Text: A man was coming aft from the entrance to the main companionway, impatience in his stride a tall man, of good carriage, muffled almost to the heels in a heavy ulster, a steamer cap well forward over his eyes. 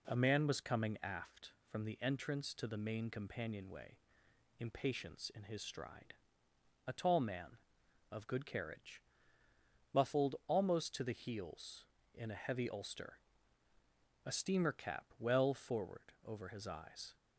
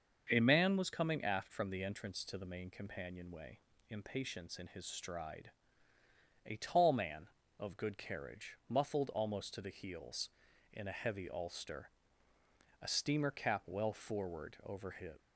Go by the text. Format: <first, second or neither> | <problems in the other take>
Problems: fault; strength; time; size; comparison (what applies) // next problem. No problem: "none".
first | starts louder than the rest; until 1.3 s; 6.5 dB // pauses between "stride" and "a"; noticeable; at 5.5 s; 0.94 s long; noticeable in the first // stops before "eyes"; at 15.1 s